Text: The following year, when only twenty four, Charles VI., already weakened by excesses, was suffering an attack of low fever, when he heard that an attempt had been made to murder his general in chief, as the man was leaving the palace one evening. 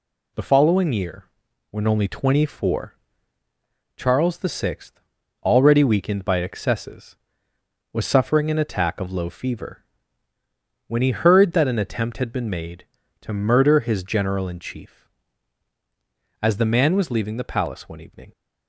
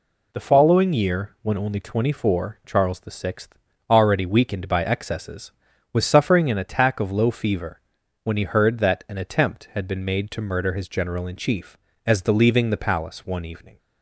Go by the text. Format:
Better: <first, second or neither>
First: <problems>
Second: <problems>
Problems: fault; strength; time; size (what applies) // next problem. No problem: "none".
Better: first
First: none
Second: skips "man was"; at 12.3 s